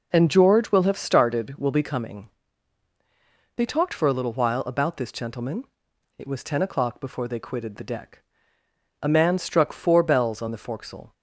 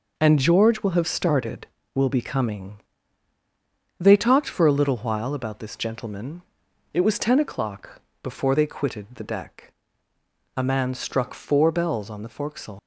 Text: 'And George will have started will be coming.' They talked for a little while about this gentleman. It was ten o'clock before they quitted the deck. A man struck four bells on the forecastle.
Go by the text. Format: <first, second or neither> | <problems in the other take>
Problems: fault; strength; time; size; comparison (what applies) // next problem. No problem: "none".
first | pauses between "o'clock" and "before"; slight; at 7.9 s; 0.22 s long // leaves "forecastle" unfinished; at 12.7 s; 110 ms